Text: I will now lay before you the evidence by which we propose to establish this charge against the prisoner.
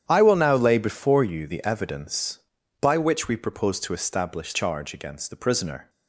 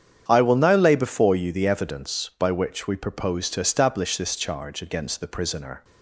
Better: second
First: starts louder than the rest; strong; until 1.0 s; 9.5 dB // skips "this"; at 4.5 s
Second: starts louder than the rest; strong; until 1.2 s; 8.5 dB

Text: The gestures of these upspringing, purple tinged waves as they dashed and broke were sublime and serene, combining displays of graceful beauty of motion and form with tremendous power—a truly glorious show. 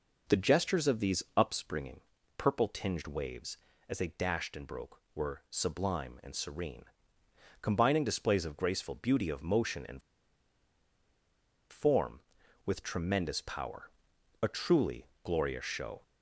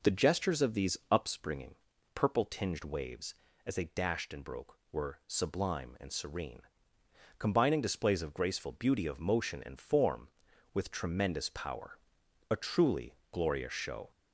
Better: second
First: pauses between "and" and "form"; strong; at 10.0 s; 1.6 s long // pauses between "truly" and "glorious"; slight; at 15.0 s; 0.16 s long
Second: pauses between "truly" and "glorious"; slight; at 13.1 s; 0.16 s long

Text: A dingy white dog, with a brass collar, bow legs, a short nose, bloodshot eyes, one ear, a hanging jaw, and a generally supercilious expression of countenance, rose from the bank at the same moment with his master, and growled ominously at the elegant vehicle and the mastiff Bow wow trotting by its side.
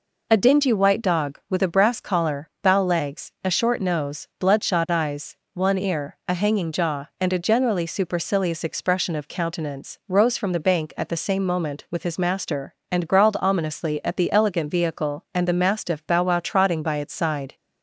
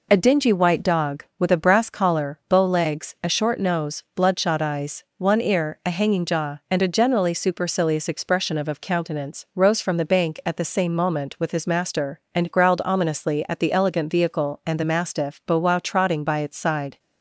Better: first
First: none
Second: says "of" twice; at 8.6 s

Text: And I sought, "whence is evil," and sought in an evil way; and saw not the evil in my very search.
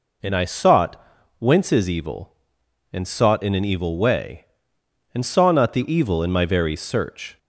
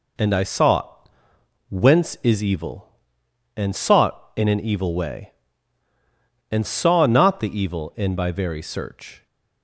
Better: first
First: none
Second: says "by" for "my"; at 8.1 s

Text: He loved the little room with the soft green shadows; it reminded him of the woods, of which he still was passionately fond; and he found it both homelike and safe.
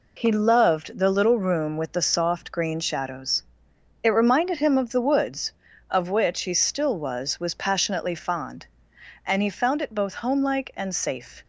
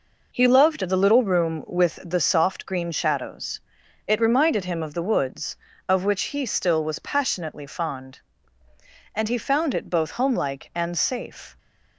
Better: second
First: says "was" twice; at 7.3 s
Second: none

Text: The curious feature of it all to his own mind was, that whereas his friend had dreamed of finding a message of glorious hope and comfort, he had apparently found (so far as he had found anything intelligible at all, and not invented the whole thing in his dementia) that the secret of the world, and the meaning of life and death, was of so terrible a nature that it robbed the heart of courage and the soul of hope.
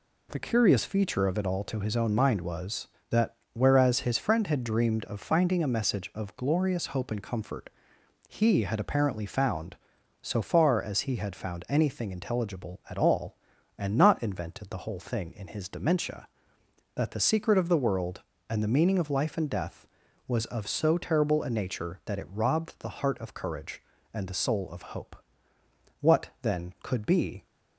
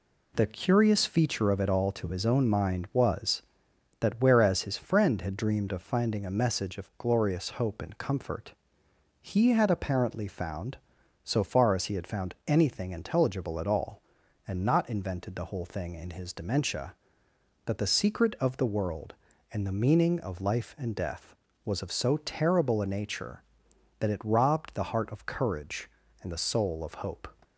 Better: second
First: pauses between "that" and "whereas"; slight; at 3.3 s; 0.20 s long // goes on to say "What then could be"; from 26.0 s on; 1.4 s long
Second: none

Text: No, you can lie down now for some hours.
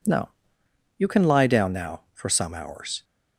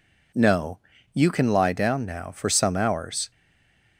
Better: first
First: none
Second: stays silent after the last word; slight; from 3.3 s on; 0.6 s long

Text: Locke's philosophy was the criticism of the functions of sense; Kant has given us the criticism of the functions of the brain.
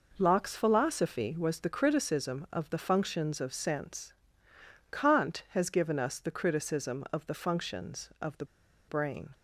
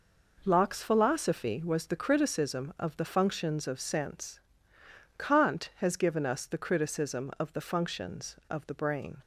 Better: second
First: pauses between "the" and "brain"; at 8.4 s; 0.42 s long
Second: none

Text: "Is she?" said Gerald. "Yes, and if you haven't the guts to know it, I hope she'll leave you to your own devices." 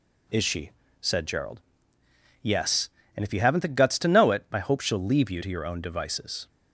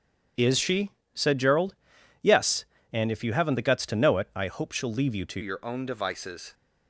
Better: first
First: none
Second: starts louder than the rest; strong; until 1.6 s; 8.5 dB // changes voice at "your"; from 5.4 s on; 1.1 s long

